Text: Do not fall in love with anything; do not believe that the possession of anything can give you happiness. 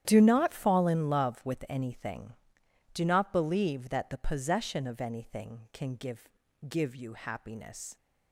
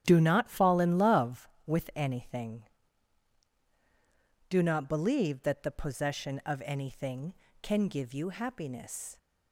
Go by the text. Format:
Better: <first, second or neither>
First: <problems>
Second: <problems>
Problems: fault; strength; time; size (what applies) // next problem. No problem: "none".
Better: second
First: starts louder than the rest; strong; until 1.0 s; 10.5 dB // says "give" twice; at 6.6 s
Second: starts louder than the rest; strong; until 1.0 s; 10 dB